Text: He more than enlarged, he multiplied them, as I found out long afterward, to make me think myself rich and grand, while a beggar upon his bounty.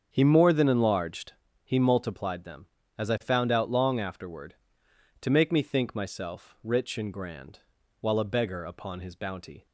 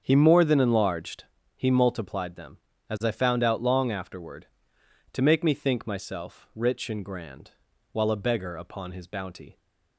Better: neither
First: starts louder than the rest; strong; until 1.1 s; 7.5 dB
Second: starts louder than the rest; strong; until 1.0 s; 7.5 dB

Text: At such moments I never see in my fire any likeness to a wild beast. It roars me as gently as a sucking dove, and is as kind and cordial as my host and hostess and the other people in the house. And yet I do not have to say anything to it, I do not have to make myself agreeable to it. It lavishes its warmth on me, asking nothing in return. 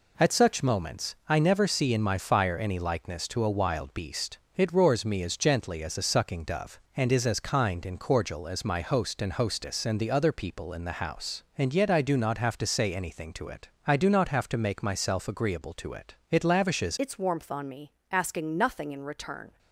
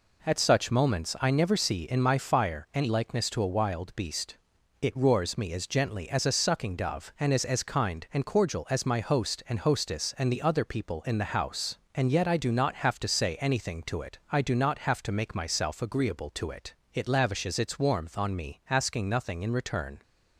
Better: second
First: changes voice at "its"; from 16.9 s on; 2.6 s long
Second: none

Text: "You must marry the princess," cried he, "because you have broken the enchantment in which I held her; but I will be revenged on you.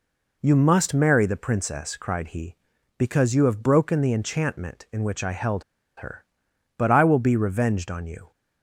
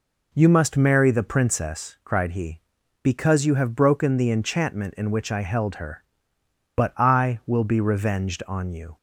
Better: second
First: pauses between "held" and "her"; slight; at 5.6 s; 0.35 s long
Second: none

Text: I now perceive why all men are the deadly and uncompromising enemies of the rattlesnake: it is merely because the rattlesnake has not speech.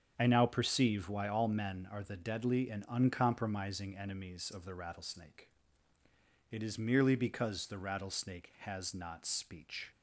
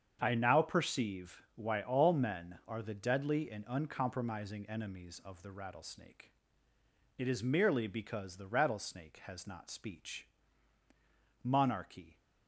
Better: first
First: starts louder than the rest; strong; until 1.1 s; 7 dB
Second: starts louder than the rest; strong; until 1.2 s; 7.5 dB // goes on to say "Monarchy"; noticeable; from 11.4 s on; 0.76 s long

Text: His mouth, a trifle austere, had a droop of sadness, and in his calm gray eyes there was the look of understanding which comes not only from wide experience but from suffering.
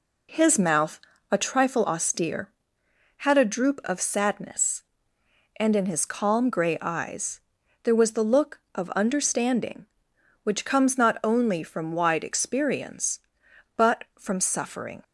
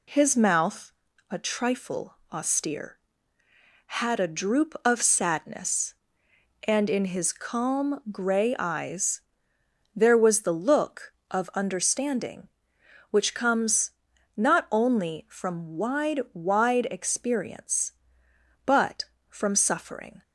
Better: first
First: pauses between "eyes" and "there"; at 7.3 s; 0.42 s long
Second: pauses between "trifle" and "austere"; slight; at 2.1 s; 0.18 s long // pauses between "eyes" and "there"; noticeable; at 9.1 s; 0.74 s long // pauses between "comes" and "not"; at 13.8 s; 0.44 s long // says "wide" twice; at 16.3 s

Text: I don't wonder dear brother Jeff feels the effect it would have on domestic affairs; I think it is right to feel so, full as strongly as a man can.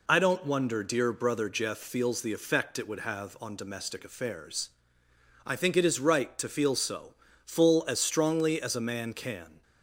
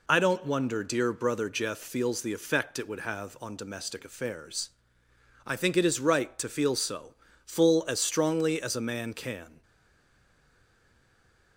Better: first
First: none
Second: stays silent after the last word; noticeable; from 9.6 s on; 1.9 s long

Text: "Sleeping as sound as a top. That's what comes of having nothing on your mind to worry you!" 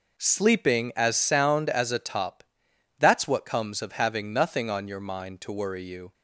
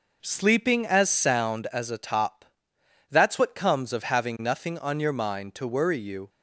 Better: neither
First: none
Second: none

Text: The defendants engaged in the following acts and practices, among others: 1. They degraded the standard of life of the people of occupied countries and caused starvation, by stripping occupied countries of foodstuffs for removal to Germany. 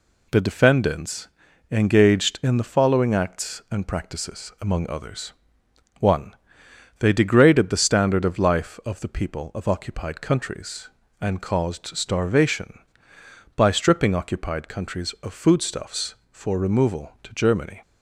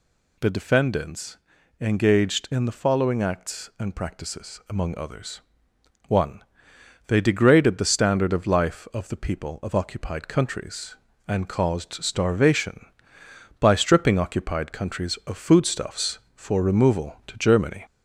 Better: first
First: pauses between "defendants" and "engaged"; at 1.2 s; 0.42 s long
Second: gets louder; slight; throughout; 2 dB // pauses between "defendants" and "engaged"; at 1.3 s; 0.42 s long

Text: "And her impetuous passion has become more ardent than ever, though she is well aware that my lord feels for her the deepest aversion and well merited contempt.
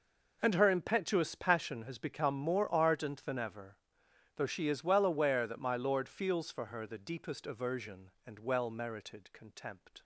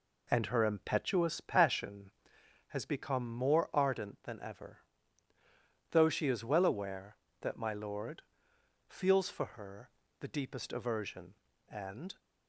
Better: first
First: none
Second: pauses between "lord" and "feels"; noticeable; at 8.2 s; 0.66 s long // pauses between "her" and "the"; slight; at 9.8 s; 0.30 s long // stops before "well merited contempt"; at 12.1 s

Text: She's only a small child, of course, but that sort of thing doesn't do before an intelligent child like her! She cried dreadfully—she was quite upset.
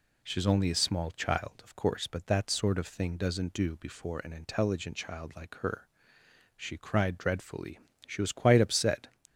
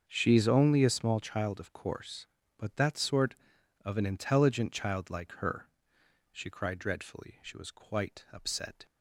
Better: first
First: none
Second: starts louder than the rest; until 1.0 s; 6.5 dB // skips "thing doesn't do before"; at 3.9 s

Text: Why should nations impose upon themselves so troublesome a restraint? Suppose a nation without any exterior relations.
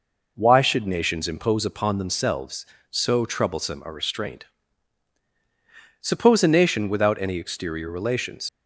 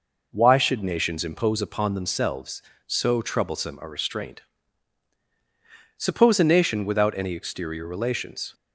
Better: second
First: leaves "relations" unfinished; at 8.4 s; 85 ms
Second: none

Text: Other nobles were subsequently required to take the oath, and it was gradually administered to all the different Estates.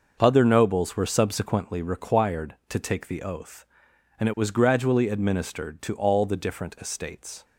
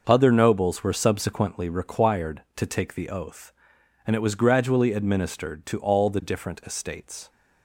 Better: neither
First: starts louder than the rest; noticeable; until 1.2 s; 6 dB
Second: starts louder than the rest; noticeable; until 1.0 s; 6 dB

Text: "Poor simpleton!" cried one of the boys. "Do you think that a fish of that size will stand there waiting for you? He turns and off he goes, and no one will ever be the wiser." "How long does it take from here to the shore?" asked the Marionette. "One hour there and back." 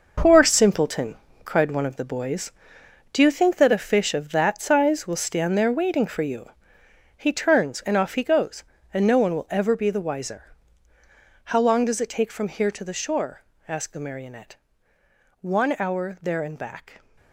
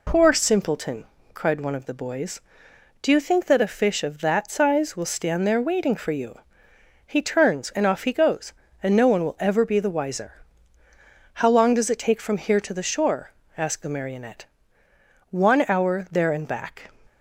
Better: second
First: gets quieter; strong; throughout; 10 dB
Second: none

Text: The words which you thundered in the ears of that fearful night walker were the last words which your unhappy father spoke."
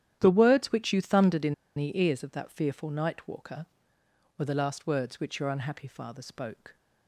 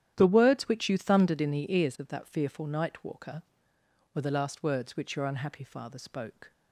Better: second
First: starts louder than the rest; strong; until 1.2 s; 11 dB // pauses between "in" and "the"; slight; at 1.5 s; 0.22 s long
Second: starts louder than the rest; strong; until 1.1 s; 11 dB

